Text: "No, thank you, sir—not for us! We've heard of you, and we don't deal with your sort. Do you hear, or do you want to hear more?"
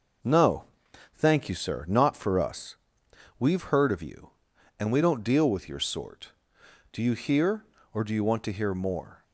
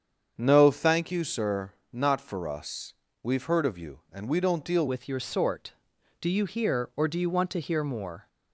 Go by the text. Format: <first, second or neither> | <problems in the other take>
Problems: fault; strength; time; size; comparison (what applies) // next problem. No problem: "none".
first | starts louder than the rest; strong; until 1.3 s; 7.5 dB // changes voice at "with"; from 4.8 s on; 3.4 s long